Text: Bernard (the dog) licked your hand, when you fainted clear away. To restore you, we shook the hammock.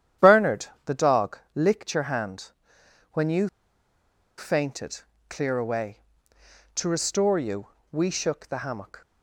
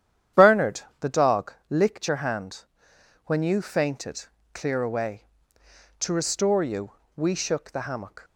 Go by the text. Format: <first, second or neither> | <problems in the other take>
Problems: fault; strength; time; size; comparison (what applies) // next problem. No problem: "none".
second | starts louder than the rest; strong; until 1.3 s; 10 dB; strong in the second // pauses between "you" and "fainted"; noticeable; at 3.4 s; 0.89 s long // pauses between "fainted" and "clear"; slight; at 5.0 s; 0.28 s long; slight in the second